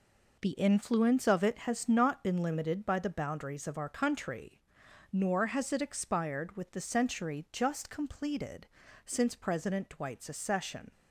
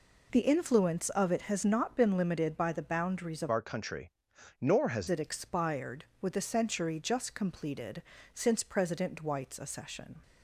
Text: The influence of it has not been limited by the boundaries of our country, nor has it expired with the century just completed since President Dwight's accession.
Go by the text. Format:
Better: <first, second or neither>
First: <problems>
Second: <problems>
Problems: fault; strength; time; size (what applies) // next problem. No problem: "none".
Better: first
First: pauses between "completed" and "since"; slight; at 8.6 s; 0.36 s long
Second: changes voice from "our" to "has"; from 3.5 to 5.0 s; 1.5 s long // pauses between "completed" and "since"; slight; at 8.0 s; 0.32 s long